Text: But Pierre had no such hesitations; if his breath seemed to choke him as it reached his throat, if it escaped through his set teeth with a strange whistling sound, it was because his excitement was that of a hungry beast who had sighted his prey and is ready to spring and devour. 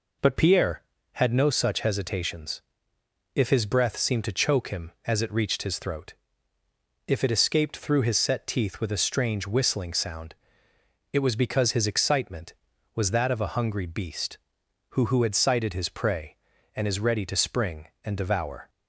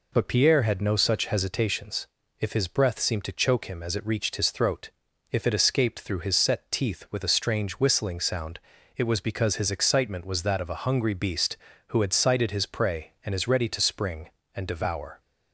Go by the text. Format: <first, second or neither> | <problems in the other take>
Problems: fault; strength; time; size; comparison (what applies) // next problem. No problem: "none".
second | says "who" twice; at 15.0 s